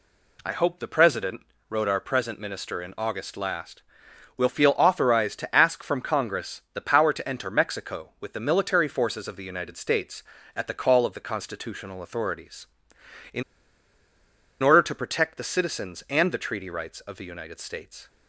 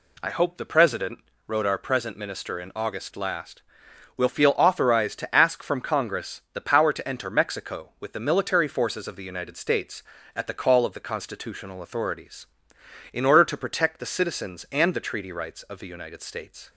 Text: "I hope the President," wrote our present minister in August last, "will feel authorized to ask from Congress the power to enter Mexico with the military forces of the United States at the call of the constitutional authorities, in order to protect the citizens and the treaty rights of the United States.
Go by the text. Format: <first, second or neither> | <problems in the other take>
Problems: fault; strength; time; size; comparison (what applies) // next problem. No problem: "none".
second | pauses between "in" and "order"; at 13.4 s; 1.1 s long